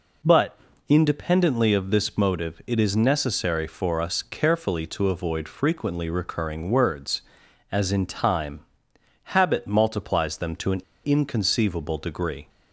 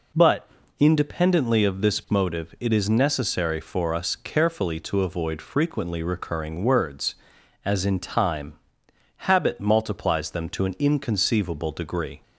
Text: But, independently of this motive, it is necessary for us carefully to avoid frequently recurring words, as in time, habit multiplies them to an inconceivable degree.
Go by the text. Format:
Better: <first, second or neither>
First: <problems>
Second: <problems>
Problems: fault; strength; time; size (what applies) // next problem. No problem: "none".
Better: second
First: pauses between "an" and "inconceivable"; slight; at 10.8 s; 0.23 s long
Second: none